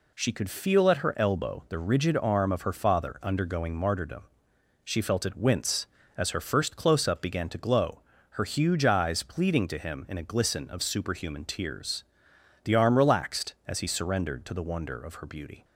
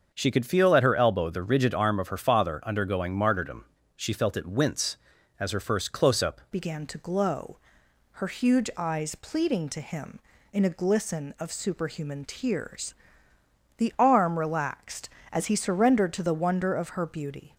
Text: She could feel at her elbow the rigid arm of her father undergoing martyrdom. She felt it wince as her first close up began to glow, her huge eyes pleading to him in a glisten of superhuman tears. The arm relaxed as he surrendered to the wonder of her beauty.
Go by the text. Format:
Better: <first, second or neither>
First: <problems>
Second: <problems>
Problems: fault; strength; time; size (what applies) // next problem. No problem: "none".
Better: first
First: none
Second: starts louder than the rest; until 1.1 s; 6.5 dB // changes voice at "began"; from 6.5 s on; 11.0 s long